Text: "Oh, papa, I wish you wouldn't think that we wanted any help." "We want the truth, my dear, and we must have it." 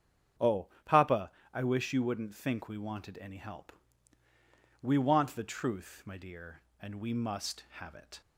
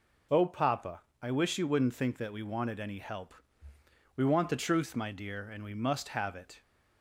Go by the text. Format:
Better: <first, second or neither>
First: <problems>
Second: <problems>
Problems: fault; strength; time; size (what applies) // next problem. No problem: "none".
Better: second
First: starts louder than the rest; strong; until 1.7 s; 8 dB // skips "that"; at 2.6 s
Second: none